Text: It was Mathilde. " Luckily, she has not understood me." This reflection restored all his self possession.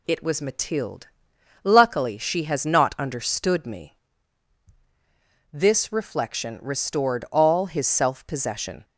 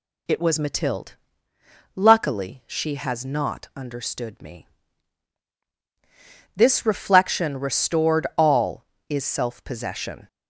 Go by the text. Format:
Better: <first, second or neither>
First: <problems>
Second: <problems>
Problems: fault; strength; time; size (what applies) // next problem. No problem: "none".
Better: first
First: none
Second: says "is" for "his"; at 9.0 s